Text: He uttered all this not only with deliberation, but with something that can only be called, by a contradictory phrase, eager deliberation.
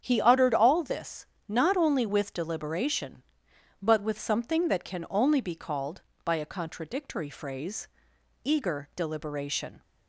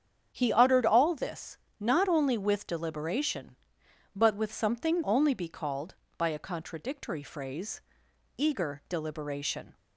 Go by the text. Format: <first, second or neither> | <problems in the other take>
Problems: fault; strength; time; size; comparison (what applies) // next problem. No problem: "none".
first | starts louder than the rest; strong; until 1.3 s; 8 dB; strong in the first // pauses between "this" and "not"; slight; at 1.5 s; 0.20 s long; slight in the first // skips "that can"; at 5.0 s